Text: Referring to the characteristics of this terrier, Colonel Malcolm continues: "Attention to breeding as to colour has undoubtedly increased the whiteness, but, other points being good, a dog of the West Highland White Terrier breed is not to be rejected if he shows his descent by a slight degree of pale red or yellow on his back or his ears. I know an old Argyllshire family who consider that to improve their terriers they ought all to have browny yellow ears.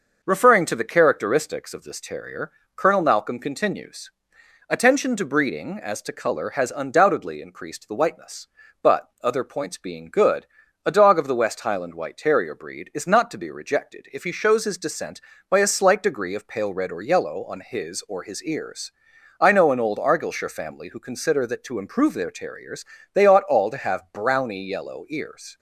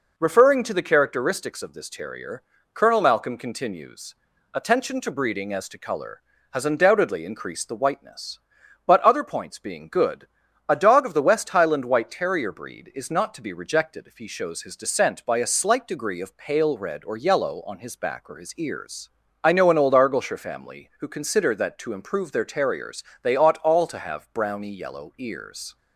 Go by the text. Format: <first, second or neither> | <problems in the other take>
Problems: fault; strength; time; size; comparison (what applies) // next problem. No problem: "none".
second | skips "back"; at 18.0 s // pauses between "terriers" and "they"; slight; at 22.8 s; 0.30 s long; slight in the second